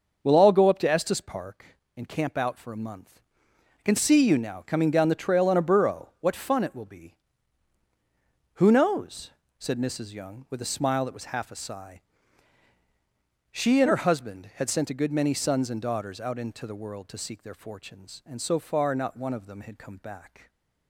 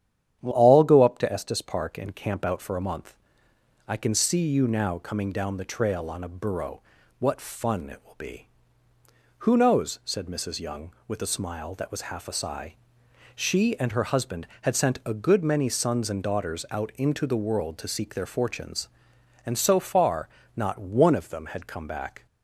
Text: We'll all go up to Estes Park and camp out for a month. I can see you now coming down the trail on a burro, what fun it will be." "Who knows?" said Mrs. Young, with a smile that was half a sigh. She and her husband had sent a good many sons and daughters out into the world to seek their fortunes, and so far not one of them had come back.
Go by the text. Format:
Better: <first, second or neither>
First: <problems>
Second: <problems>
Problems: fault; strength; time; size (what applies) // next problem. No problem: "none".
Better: first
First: starts louder than the rest; noticeable; until 1.2 s; 6 dB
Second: starts louder than the rest; strong; until 1.4 s; 10 dB // changes voice at "all"; from 0.5 s on; 21.7 s long // pauses between "far" and "not"; slight; at 20.2 s; 0.30 s long